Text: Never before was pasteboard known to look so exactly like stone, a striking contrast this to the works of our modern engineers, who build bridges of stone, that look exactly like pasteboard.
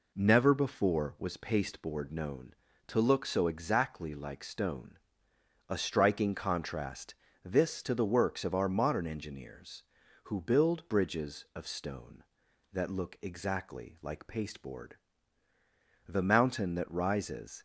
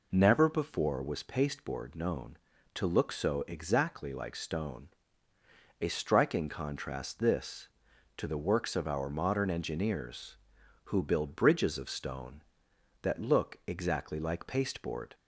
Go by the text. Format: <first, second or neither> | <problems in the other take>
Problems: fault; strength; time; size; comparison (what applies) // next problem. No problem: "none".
second | pauses between "contrast" and "this"; slight; at 7.1 s; 0.30 s long // goes on to say "The mountain that rises"; from 16.0 s on; 1.5 s long